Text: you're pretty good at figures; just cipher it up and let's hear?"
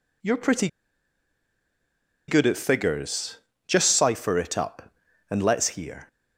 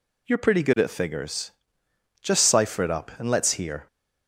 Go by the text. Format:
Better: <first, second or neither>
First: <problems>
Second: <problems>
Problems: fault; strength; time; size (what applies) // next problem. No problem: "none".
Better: second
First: pauses between "pretty" and "good"; strong; at 0.6 s; 1.6 s long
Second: none